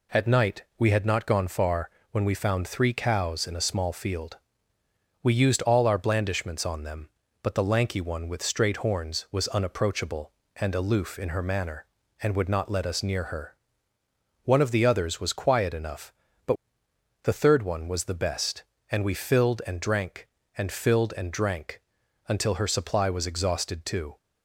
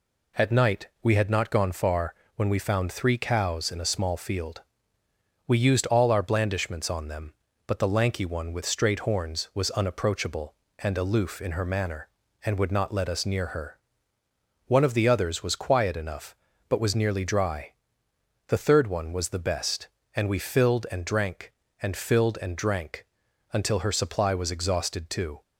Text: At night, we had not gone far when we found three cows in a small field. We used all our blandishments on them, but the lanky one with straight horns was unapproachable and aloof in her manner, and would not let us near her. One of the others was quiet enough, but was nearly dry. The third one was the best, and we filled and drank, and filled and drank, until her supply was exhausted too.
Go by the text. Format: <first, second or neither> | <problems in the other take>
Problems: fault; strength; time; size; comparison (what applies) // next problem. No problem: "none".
second | pauses between "far" and "when"; slight; at 1.9 s; 0.22 s long; slight in the second // skips "was nearly dry"; at 16.8 s